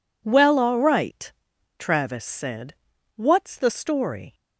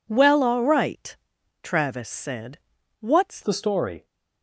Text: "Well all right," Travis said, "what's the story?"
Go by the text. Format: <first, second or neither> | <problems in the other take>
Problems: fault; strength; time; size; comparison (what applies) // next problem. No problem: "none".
first | changes voice at "the"; from 3.4 s on; 0.6 s long